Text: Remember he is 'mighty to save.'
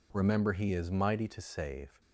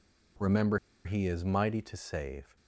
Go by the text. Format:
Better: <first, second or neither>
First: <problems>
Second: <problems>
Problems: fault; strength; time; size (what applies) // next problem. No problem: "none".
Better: first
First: none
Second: pauses between "Remember" and "he"; slight; at 0.7 s; 0.27 s long